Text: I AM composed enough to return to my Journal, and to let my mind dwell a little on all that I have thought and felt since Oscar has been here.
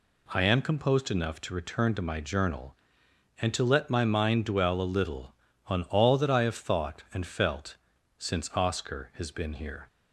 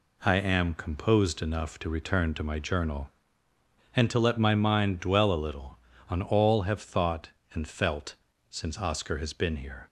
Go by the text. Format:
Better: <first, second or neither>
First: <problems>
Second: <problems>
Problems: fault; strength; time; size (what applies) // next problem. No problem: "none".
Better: first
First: pauses between "felt" and "since"; at 7.7 s; 0.42 s long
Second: skips "that I"; at 6.6 s // pauses between "felt" and "since"; slight; at 8.1 s; 0.34 s long